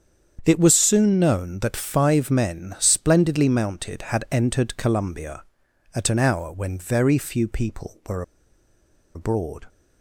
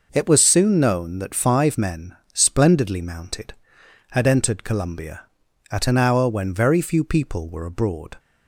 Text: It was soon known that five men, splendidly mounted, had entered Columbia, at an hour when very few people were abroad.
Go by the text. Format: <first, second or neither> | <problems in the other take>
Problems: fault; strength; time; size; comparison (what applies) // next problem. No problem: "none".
second | starts louder than the rest; strong; until 1.4 s; 7.5 dB // pauses between "were" and "abroad"; noticeable; at 8.2 s; 0.93 s long